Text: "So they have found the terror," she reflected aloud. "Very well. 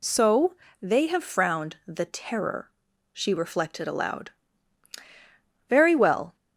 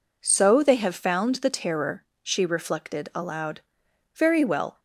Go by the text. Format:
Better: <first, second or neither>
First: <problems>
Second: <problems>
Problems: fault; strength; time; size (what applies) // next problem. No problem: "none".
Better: second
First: pauses between "So" and "they"; slight; at 0.5 s; 0.28 s long // says "frowned" for "found"; at 1.2 s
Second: none